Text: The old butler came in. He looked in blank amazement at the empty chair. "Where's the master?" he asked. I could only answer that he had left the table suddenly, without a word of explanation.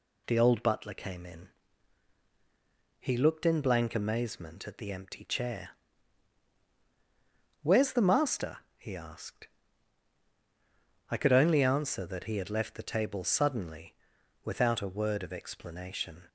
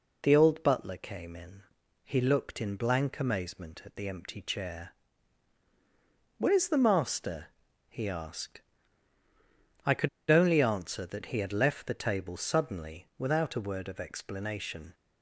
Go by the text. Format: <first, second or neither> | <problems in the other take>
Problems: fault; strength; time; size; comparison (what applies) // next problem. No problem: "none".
first | pauses between "could" and "only"; slight; at 10.0 s; 0.20 s long